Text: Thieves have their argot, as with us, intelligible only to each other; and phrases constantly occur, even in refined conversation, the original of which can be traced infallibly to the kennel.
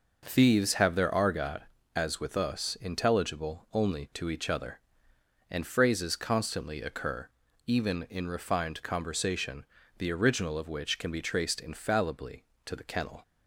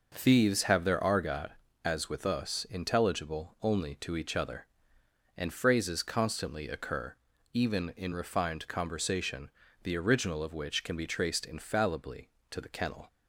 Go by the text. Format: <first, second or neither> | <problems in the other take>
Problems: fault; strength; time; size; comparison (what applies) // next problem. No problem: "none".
neither | none